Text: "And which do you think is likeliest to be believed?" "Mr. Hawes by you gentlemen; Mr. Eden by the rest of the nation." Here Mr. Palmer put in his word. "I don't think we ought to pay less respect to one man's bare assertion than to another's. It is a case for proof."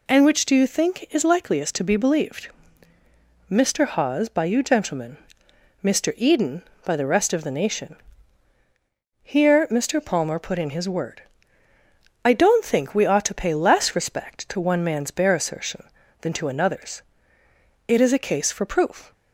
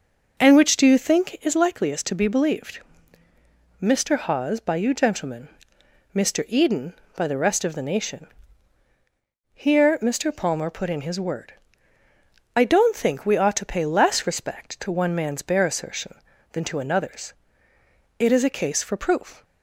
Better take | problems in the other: first | starts louder than the rest; noticeable; until 1.5 s; 5.5 dB

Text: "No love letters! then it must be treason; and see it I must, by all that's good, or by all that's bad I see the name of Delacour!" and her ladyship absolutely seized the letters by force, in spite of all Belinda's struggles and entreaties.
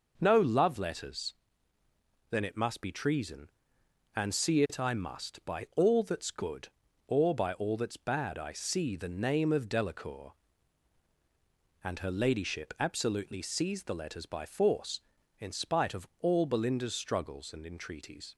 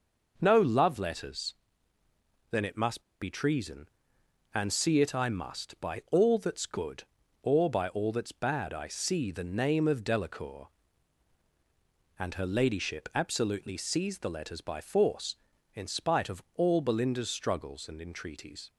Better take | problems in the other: first | pauses between "must" and "be"; slight; at 2.9 s; 0.20 s long

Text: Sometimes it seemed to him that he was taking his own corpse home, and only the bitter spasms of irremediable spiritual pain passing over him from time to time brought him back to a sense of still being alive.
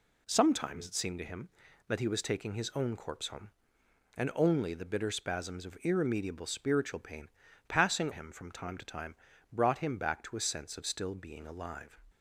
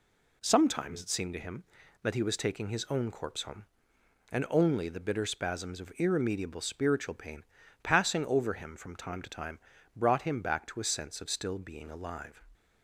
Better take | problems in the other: second | pauses between "pain" and "passing"; at 7.2 s; 0.40 s long; also in the second // skips "over"; at 8.1 s // pauses between "time" and "brought"; slight; at 9.1 s; 0.36 s long; slight in the second

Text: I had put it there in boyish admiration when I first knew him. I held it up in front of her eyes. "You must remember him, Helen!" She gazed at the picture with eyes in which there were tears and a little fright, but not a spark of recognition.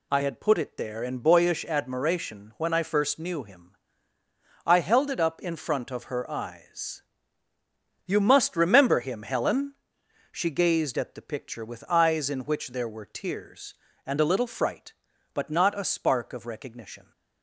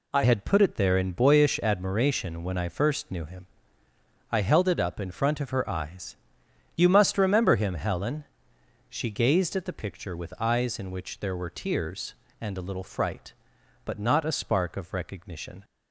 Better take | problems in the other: first | changes voice at "had"; from 0.2 s on; 15.4 s long

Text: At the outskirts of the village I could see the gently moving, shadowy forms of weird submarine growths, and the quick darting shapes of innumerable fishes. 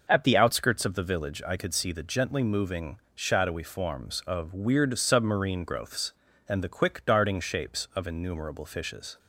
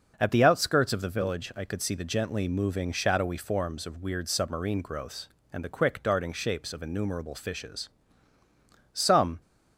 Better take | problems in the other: first | starts louder than the rest; noticeable; until 1.1 s; 6 dB // goes on to say "Some"; slight; from 8.9 s on; 0.48 s long

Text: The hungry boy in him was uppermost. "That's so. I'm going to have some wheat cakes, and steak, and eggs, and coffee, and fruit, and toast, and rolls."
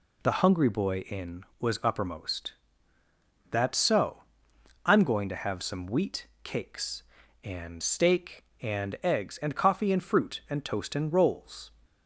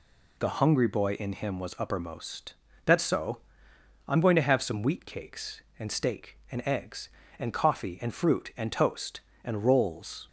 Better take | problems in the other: second | skips "him"; at 1.5 s // pauses between "wheat" and "cakes"; slight; at 6.2 s; 0.16 s long

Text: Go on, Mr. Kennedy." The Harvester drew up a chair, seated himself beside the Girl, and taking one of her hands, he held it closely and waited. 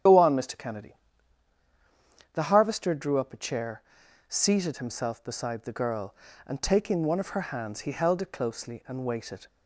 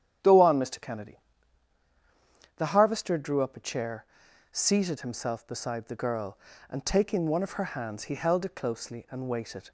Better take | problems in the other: second | loses the start of "Go"; at 0.0 s; 65 ms // starts louder than the rest; strong; until 2.4 s; 8 dB; strong in the second

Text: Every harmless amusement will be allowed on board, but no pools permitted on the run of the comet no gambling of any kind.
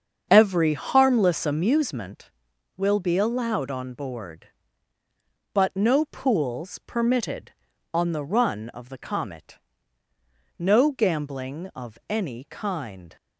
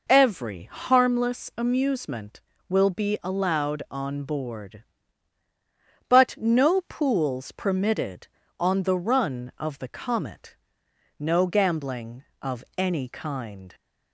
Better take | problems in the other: second | starts louder than the rest; strong; until 2.1 s; 7 dB // pauses between "comet" and "no"; at 9.5 s; 1.0 s long; noticeable in the second

